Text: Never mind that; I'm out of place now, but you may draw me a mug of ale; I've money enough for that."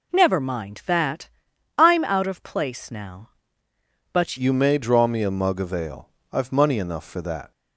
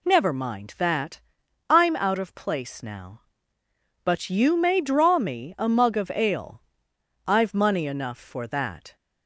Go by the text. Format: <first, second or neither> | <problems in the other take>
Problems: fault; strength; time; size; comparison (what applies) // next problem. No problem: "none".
second | changes voice at "you"; from 4.3 s on; 3.2 s long